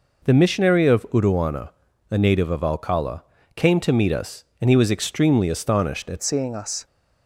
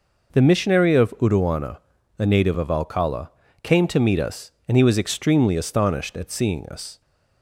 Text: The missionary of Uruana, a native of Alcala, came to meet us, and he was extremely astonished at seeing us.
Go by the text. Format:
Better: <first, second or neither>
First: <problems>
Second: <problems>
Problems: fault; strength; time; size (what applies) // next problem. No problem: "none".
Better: second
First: changes voice at "seeing"; from 6.2 s on; 0.6 s long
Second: none